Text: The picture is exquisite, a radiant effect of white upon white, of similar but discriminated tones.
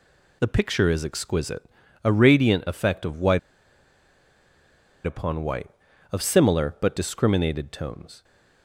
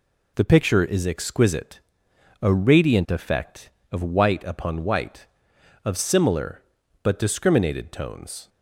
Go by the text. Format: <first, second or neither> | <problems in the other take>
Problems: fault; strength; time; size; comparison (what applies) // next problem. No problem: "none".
second | pauses between "white" and "upon"; strong; at 3.3 s; 1.6 s long